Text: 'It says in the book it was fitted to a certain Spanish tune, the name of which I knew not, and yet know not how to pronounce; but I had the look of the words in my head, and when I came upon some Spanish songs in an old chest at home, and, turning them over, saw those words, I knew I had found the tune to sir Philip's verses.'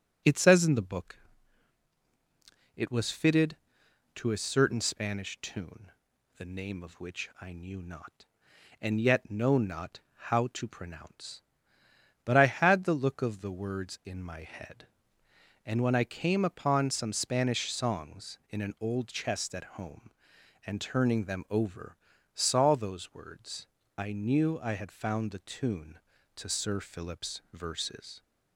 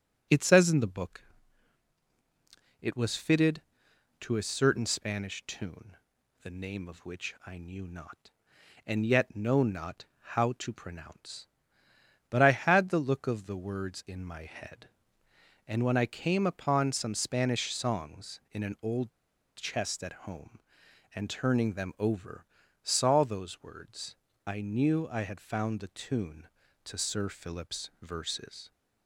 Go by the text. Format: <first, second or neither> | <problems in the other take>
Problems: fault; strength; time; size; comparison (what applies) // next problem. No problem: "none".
first | pauses between "book" and "it"; strong; at 1.2 s; 1.5 s long; strong in the first // pauses between "not" and "how"; slight; at 10.0 s; 0.16 s long; slight in the first // pauses between "old" and "chest"; noticeable; at 19.0 s; 0.49 s long